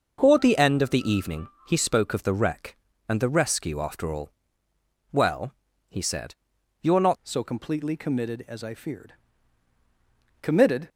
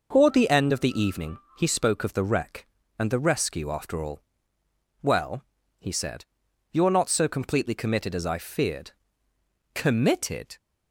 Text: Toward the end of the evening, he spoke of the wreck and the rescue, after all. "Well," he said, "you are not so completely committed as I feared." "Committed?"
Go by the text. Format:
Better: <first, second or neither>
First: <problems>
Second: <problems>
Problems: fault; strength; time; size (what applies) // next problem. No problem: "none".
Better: second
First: changes voice at "so"; from 7.2 s on; 3.6 s long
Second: none